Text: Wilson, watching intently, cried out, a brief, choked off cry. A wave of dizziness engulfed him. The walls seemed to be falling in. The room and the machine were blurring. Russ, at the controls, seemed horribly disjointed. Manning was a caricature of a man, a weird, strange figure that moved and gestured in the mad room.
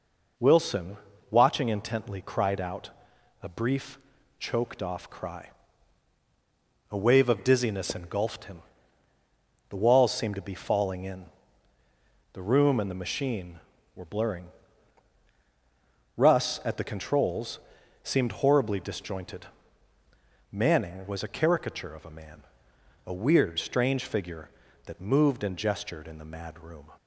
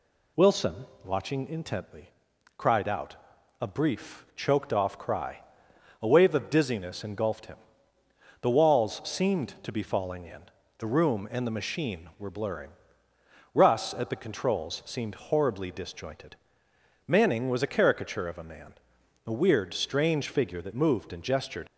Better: first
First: none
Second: stops before "in the mad room"; at 21.6 s

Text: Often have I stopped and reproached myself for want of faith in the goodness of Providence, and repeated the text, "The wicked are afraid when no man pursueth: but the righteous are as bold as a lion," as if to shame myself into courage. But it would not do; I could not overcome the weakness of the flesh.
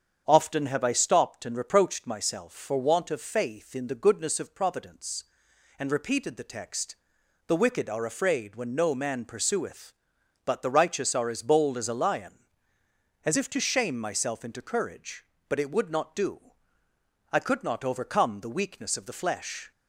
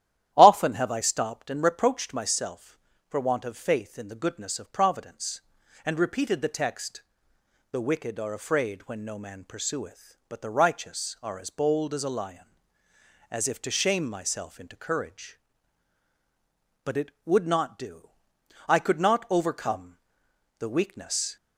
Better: first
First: starts louder than the rest; strong; until 1.2 s; 7.5 dB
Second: starts louder than the rest; strong; until 1.3 s; 12 dB // pauses between "overcome" and "the"; noticeable; at 19.9 s; 0.62 s long // stops before "of the flesh"; at 21.3 s

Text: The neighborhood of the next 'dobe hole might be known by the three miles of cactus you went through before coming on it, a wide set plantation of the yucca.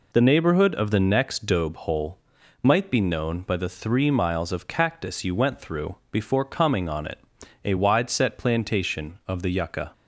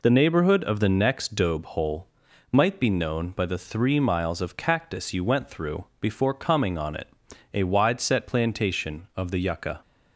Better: neither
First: pauses between "hole" and "might"; at 2.1 s; 0.44 s long // pauses between "through" and "before"; slight; at 5.9 s; 0.16 s long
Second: pauses between "hole" and "might"; at 2.0 s; 0.44 s long // pauses between "through" and "before"; slight; at 5.8 s; 0.16 s long

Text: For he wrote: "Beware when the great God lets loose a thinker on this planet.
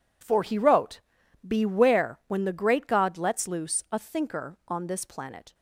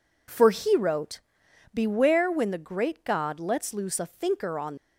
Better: first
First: none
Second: stops before "this planet"; at 4.7 s

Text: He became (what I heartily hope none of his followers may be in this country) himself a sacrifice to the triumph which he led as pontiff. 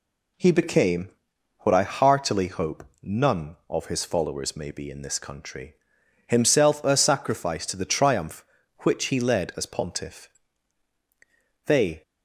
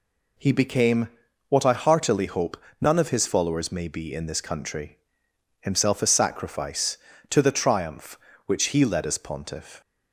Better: second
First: pauses between "hope" and "none"; slight; at 2.8 s; 0.20 s long // goes on to say "They"; slight; from 11.6 s on; 0.36 s long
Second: pauses between "hope" and "none"; slight; at 2.5 s; 0.20 s long

